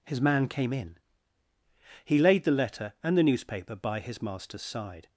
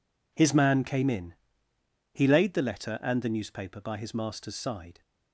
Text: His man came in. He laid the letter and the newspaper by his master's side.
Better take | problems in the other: first | gets quieter; strong; throughout; 14 dB

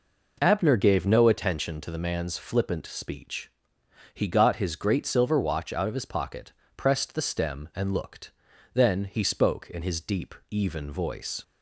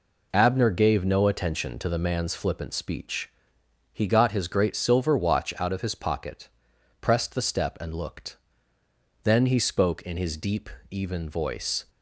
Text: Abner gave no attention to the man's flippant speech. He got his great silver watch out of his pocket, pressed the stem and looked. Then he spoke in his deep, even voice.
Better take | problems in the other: first | says "step" for "stem"; at 7.4 s

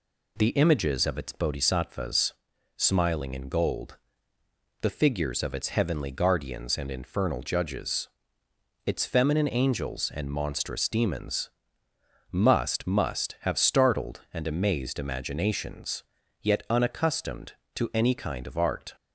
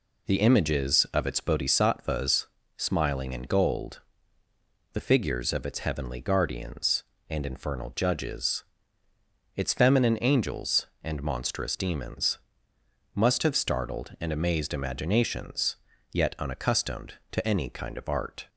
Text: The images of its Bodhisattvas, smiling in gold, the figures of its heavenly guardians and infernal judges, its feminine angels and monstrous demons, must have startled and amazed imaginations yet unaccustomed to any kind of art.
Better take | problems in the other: second | says "must" twice; at 12.8 s // pauses between "imaginations" and "yet"; at 16.0 s; 0.38 s long; slight in the second

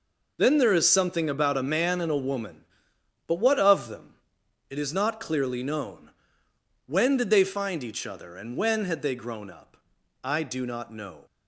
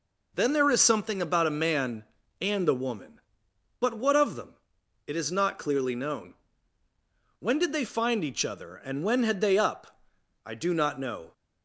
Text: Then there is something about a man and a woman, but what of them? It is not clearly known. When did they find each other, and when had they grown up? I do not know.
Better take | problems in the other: first | skips "grown"; at 9.5 s

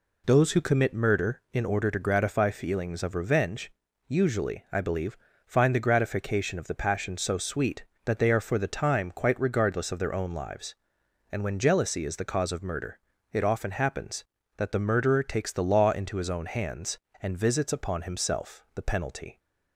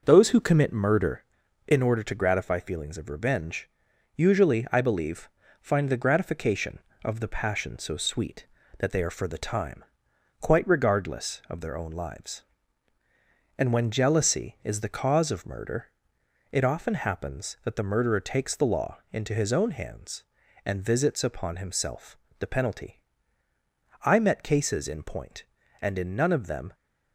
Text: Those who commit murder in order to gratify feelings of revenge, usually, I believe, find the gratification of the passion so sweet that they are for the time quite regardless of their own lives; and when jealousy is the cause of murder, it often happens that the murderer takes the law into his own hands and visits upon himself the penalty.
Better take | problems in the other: first | pauses between "time" and "quite"; noticeable; at 9.8 s; 0.56 s long // pauses between "himself" and "the"; slight; at 22.1 s; 0.22 s long // goes on to say "I met cases in point and in none of them"; strong; from 24.0 s on; 2.7 s long

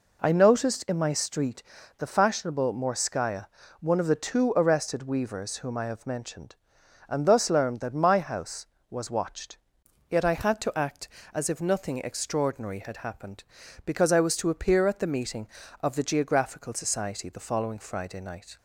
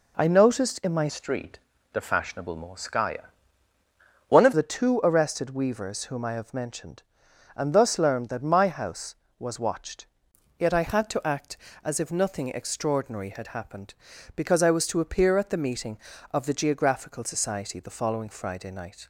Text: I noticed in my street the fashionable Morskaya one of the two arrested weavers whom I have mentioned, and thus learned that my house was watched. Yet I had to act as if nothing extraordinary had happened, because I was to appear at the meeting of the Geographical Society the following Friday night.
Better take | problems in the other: first | changes voice from "street" to "of"; from 1.0 to 4.5 s; 3.5 s long // pauses between "street" and "the"; slight; at 1.5 s; 0.34 s long; slight in the first // pauses between "Morskaya" and "one"; noticeable; at 3.3 s; 0.96 s long; slight in the first

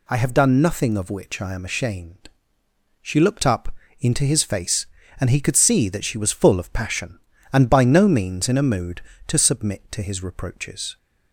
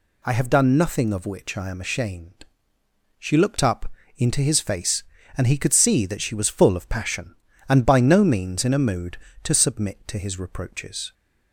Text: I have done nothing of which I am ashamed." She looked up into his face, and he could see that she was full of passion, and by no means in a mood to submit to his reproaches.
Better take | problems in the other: neither | pauses between "up" and "into"; slight; the same in both

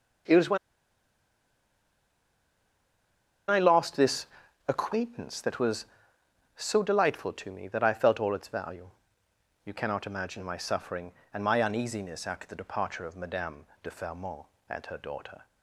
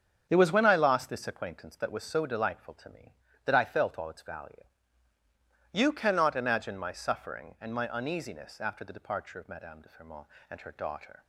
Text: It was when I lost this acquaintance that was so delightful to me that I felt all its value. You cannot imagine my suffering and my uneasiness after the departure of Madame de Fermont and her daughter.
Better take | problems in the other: second | starts louder than the rest; strong; until 4.2 s; 7.5 dB; strong in the second // pauses between "when" and "I"; strong; at 0.5 s; 2.9 s long // pauses between "this" and "acquaintance"; at 4.2 s; 0.42 s long // pauses between "Madame" and "de"; slight; at 13.6 s; 0.18 s long

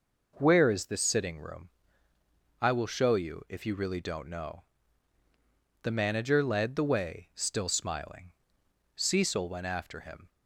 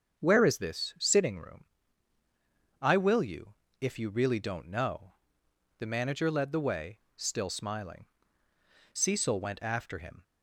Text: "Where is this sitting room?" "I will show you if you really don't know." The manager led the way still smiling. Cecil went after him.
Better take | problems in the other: first | starts louder than the rest; until 1.2 s; 7 dB // skips "show"; at 3.2 s // pauses between "you" and "if"; slight; at 3.5 s; 0.28 s long // pauses between "way" and "still"; slight; at 6.9 s; 0.18 s long

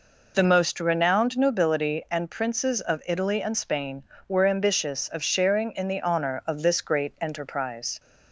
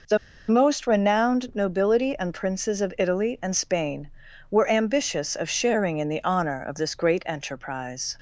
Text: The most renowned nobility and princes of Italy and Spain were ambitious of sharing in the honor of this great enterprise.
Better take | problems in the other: first | pauses between "The" and "most"; slight; at 0.1 s; 0.31 s long

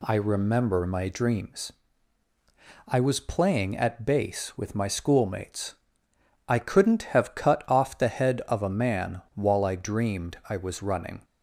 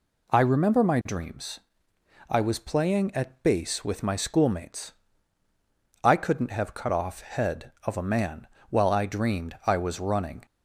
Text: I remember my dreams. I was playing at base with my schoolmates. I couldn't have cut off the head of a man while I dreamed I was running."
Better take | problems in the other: first | skips "the"; at 7.1 s // pauses between "man" and "while"; slight; at 8.4 s; 0.22 s long

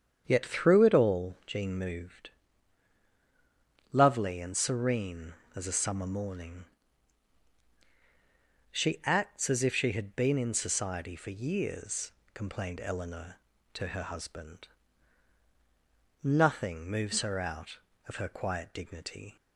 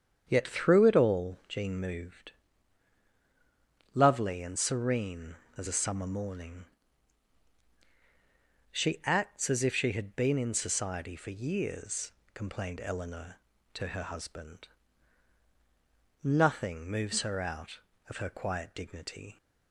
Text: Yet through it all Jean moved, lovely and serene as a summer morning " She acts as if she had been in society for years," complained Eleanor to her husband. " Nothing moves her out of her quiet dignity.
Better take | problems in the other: neither | starts louder than the rest; strong; the same in both

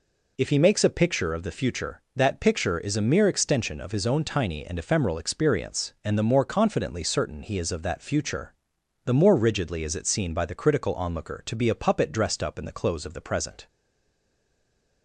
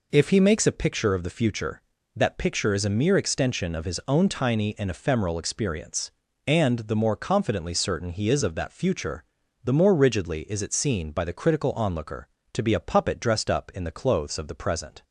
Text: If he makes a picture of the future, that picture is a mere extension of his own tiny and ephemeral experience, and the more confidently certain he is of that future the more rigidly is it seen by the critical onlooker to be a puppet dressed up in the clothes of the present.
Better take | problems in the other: second | pauses between "future" and "the"; noticeable; at 8.5 s; 0.50 s long; also in the second // stays silent after the last word; noticeable; from 13.6 s on; 1.4 s long

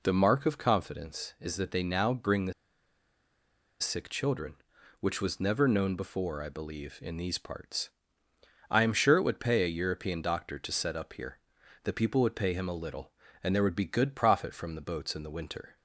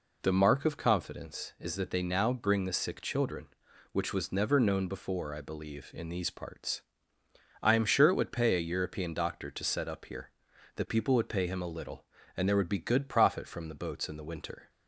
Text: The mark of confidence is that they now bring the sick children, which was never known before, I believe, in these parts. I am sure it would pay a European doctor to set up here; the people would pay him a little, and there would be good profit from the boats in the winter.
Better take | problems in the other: second | pauses between "the" and "sick"; strong; at 2.5 s; 1.2 s long

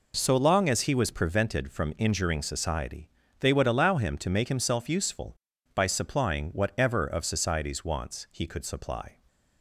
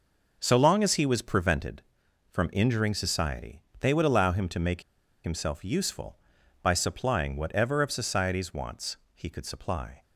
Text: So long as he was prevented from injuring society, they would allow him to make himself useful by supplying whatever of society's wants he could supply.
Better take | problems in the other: first | pauses between "make" and "himself"; at 4.8 s; 0.41 s long // pauses between "wants" and "he"; slight; at 8.9 s; 0.18 s long

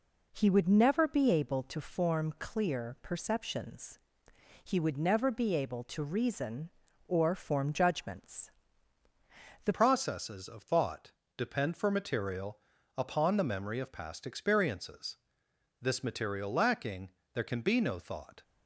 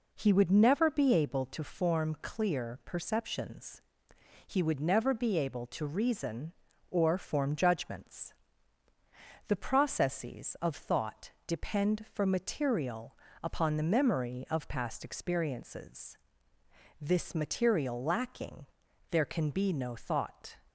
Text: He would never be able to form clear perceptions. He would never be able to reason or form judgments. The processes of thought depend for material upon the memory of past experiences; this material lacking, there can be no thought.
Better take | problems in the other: second | changes voice at "processes"; from 9.7 s on; 8.7 s long // pauses between "thought" and "depend"; slight; at 11.1 s; 0.24 s long; slight in the second // pauses between "material" and "upon"; at 12.5 s; 0.38 s long; slight in the second

